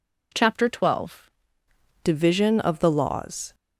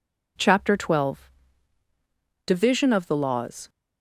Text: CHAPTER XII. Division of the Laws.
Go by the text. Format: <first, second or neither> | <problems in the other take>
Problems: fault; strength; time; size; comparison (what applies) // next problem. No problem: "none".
second | changes voice at "Division"; from 2.0 s on; 1.5 s long